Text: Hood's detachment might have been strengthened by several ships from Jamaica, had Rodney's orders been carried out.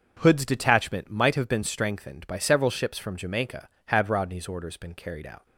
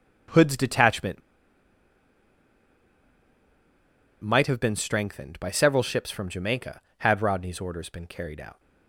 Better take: first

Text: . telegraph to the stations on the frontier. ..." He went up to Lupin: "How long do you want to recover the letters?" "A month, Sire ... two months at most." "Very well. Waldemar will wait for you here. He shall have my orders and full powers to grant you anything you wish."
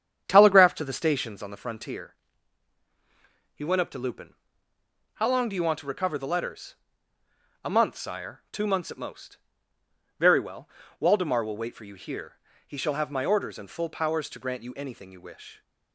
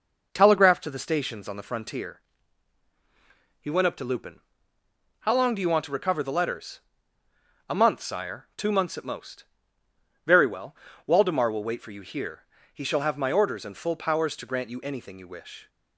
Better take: second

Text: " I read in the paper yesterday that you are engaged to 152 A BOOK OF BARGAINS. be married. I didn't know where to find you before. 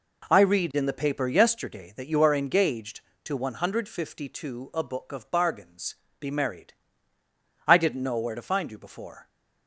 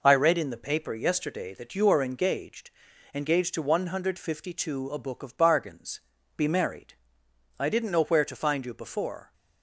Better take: first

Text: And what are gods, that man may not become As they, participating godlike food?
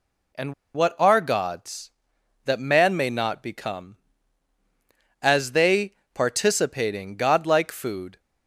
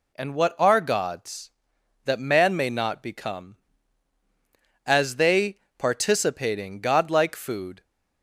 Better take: second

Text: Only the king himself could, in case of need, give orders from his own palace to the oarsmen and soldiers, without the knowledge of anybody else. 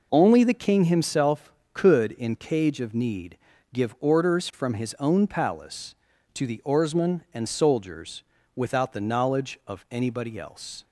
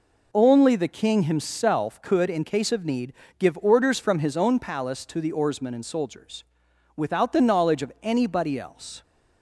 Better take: second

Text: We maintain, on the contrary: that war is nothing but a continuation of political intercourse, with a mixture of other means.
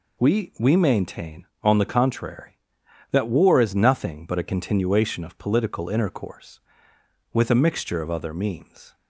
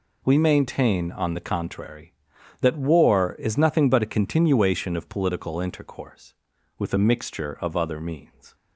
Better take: second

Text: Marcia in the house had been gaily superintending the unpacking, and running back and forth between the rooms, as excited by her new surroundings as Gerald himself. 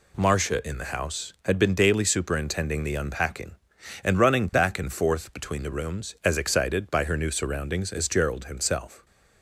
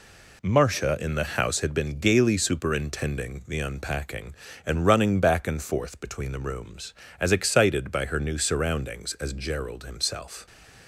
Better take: second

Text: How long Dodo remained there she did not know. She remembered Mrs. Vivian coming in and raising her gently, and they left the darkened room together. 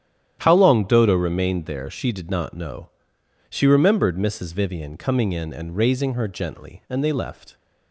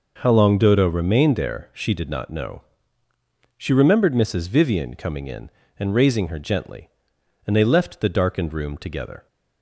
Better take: second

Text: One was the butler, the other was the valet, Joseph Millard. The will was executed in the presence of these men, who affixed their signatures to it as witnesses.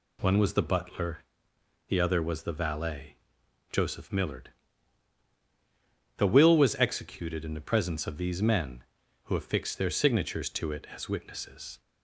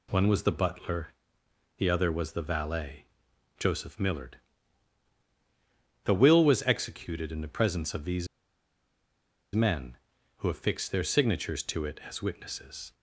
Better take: first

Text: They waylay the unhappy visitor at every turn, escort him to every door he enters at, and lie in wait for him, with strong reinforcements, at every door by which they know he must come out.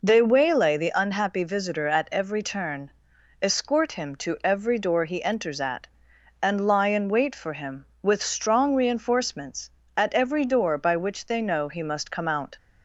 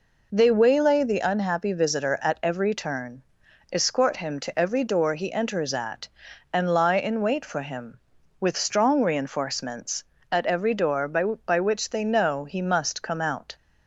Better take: first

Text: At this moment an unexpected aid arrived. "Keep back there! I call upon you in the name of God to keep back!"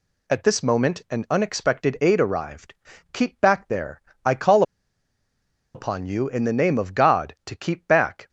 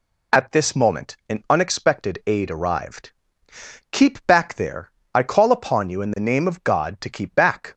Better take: second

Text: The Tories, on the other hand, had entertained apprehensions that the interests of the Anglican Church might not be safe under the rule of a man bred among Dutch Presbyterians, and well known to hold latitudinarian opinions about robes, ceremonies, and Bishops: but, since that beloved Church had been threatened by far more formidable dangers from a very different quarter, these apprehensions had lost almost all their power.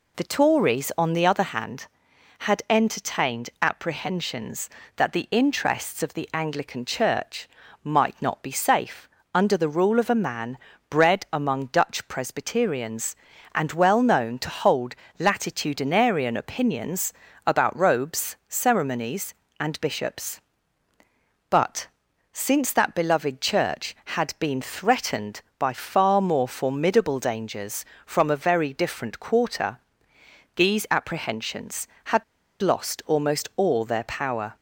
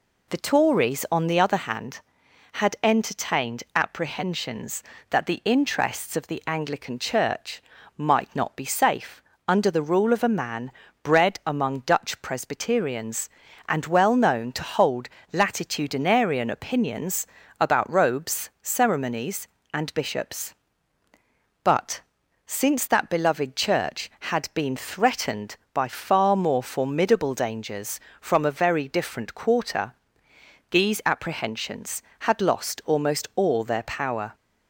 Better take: second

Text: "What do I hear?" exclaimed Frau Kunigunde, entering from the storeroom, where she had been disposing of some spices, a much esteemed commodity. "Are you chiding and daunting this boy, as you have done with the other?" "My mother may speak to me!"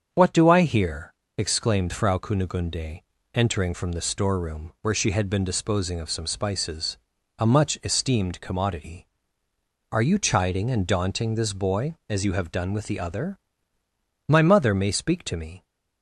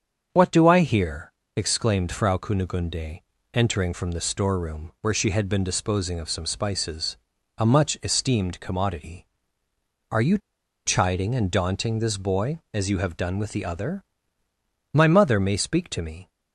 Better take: first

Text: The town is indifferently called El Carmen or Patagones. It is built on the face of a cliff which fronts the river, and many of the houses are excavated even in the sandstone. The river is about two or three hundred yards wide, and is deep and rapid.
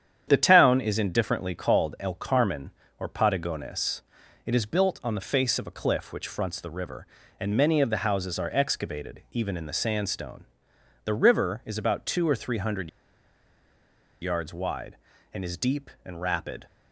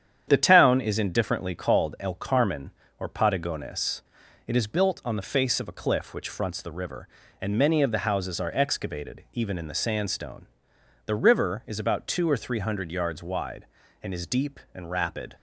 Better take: second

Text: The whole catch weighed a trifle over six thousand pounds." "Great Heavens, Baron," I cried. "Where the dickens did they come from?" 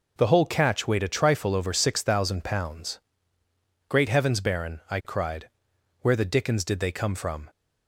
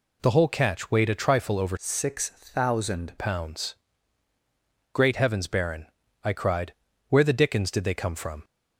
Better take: first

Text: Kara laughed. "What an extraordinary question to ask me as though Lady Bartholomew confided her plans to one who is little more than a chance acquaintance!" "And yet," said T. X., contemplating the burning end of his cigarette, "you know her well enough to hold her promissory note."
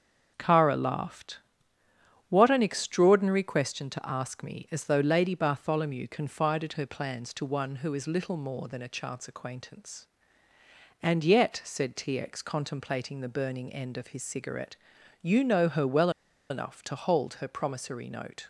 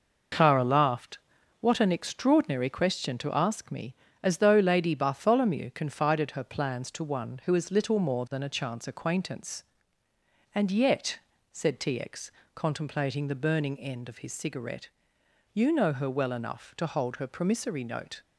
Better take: second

